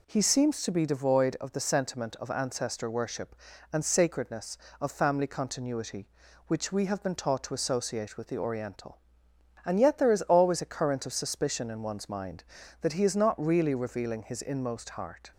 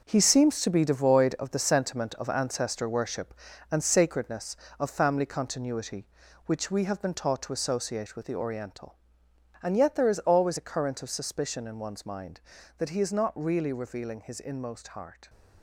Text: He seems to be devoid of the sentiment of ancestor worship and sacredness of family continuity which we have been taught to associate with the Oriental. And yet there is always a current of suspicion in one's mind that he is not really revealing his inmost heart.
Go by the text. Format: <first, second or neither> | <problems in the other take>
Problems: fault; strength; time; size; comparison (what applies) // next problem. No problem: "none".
first | gets quieter; strong; throughout; 9 dB